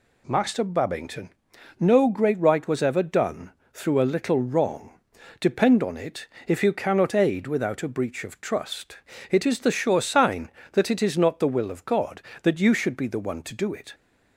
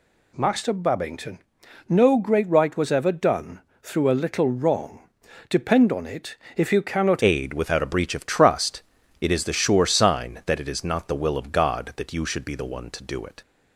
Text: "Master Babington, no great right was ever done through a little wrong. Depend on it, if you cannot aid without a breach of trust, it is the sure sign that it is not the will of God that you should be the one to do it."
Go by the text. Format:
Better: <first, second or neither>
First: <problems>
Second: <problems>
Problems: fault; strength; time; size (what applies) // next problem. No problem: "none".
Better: first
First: pauses between "done" and "through"; slight; at 3.5 s; 0.24 s long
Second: pauses between "done" and "through"; slight; at 3.6 s; 0.24 s long // changes voice at "aid"; from 7.2 s on; 6.2 s long